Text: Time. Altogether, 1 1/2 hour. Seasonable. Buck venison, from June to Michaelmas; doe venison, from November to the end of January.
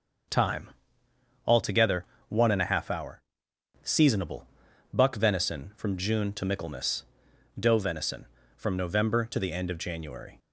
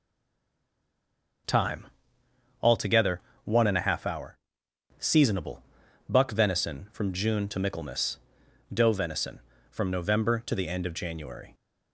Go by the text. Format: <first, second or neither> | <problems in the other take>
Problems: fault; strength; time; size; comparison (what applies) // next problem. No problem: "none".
first | stays silent before the first word; noticeable; until 1.4 s; 1.4 s long // starts louder than the rest; noticeable; until 3.4 s; 6 dB; also in the first